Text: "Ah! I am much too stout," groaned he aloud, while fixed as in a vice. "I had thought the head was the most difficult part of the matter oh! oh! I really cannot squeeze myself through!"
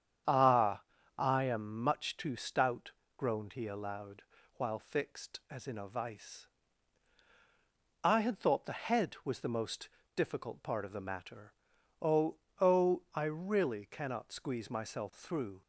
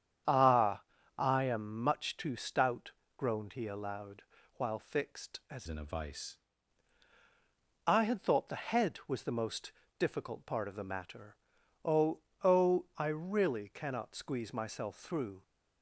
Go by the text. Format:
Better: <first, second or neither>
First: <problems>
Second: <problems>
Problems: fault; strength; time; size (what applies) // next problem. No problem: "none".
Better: first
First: starts louder than the rest; strong; until 1.6 s; 8.5 dB // pauses between "most" and "difficult"; slight; at 9.8 s; 0.28 s long // pauses between "matter" and "oh"; noticeable; at 11.5 s; 0.48 s long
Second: starts louder than the rest; strong; until 1.6 s; 8.5 dB // changes voice from "in" to "vice"; from 5.6 to 6.3 s; 0.7 s long // pauses between "most" and "difficult"; slight; at 9.7 s; 0.28 s long // pauses between "matter" and "oh"; noticeable; at 11.3 s; 0.48 s long